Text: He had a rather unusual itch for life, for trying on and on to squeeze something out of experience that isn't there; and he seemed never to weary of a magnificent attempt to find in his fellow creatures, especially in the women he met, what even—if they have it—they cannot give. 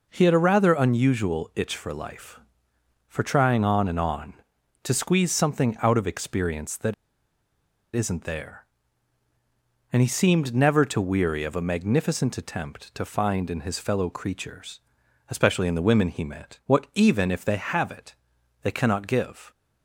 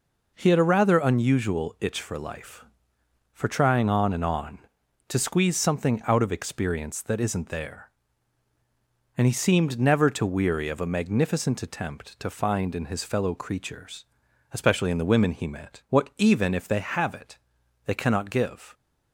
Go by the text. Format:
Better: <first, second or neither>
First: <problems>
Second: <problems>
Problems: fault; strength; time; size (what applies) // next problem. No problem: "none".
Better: second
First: pauses between "that" and "isn't"; at 6.9 s; 1.0 s long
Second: none